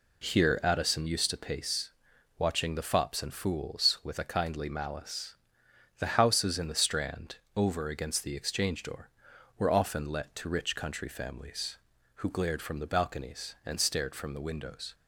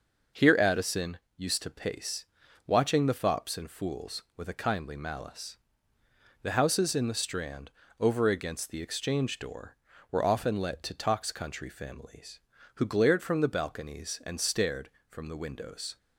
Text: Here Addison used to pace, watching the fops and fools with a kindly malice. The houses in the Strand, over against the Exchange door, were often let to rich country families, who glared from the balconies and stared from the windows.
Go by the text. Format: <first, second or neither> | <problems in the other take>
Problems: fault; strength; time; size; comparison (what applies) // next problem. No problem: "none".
first | pauses between "Addison" and "used"; slight; at 1.1 s; 0.18 s long // says "tox" for "rich"; at 10.9 s